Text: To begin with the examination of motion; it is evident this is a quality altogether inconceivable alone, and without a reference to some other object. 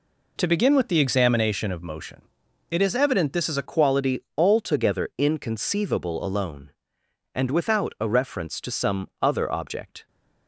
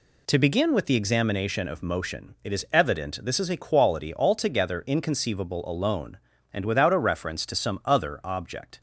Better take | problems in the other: second | changes voice at "quality"; from 3.6 s on; 6.4 s long // pauses between "quality" and "altogether"; slight; at 4.1 s; 0.18 s long

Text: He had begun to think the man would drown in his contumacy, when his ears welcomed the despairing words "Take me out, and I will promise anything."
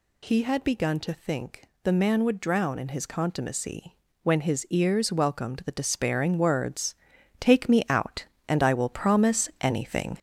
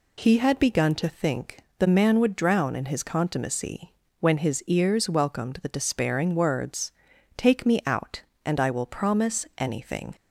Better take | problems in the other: second | gets louder; noticeable; throughout; 5.5 dB // pauses between "think" and "the"; slight; at 1.6 s; 0.20 s long; slight in the second // pauses between "words" and "Take"; noticeable; at 6.9 s; 0.46 s long; noticeable in the second

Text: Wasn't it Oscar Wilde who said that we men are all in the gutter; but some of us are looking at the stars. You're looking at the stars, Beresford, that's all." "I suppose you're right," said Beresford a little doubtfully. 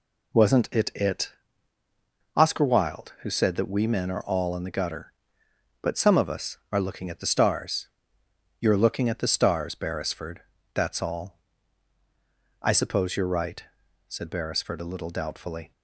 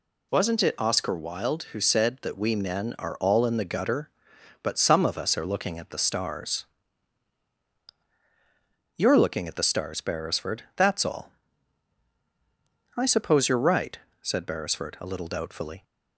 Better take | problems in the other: second | says "it" twice; at 0.9 s

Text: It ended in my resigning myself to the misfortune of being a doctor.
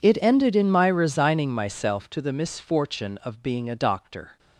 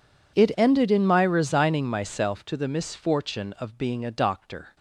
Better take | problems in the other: neither | none

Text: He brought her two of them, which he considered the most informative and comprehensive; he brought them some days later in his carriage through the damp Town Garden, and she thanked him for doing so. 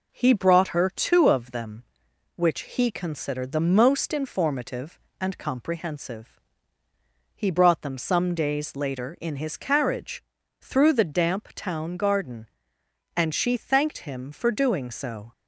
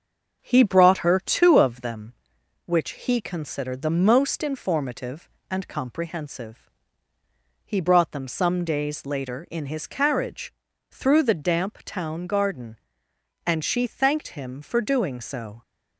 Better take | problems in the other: first | starts louder than the rest; until 2.0 s; 6.5 dB // pauses between "carriage" and "through"; at 10.5 s; 0.38 s long; also in the first

